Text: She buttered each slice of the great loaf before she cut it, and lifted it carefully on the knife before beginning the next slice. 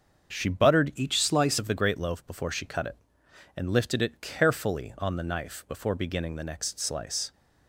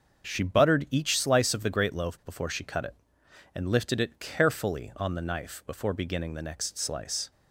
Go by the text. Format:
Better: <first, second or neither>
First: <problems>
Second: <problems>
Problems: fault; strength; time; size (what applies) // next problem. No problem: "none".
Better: second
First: starts louder than the rest; until 1.3 s; 6.5 dB // changes voice from "each" to "slice"; from 0.9 to 1.5 s; 0.6 s long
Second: starts louder than the rest; until 1.2 s; 6.5 dB